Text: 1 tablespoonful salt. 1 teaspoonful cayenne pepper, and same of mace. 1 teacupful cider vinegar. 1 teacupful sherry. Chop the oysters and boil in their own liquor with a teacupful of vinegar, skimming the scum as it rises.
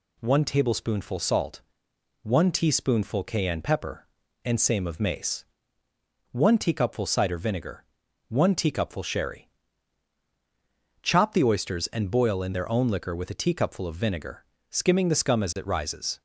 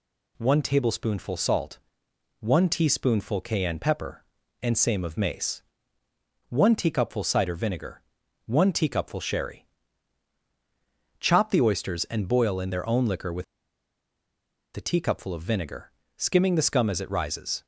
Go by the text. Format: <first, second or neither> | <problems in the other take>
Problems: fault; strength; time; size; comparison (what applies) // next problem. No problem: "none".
first | pauses between "with" and "a"; strong; at 13.4 s; 1.3 s long